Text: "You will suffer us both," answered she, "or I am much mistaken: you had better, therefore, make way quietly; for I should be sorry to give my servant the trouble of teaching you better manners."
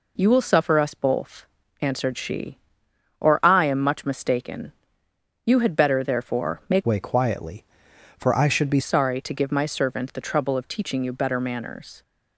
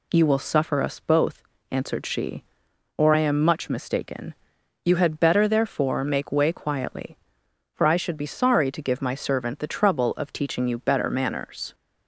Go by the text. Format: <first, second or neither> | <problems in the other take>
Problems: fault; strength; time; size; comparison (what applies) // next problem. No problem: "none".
second | changes voice from "way" to "be"; from 6.8 to 8.8 s; 2.0 s long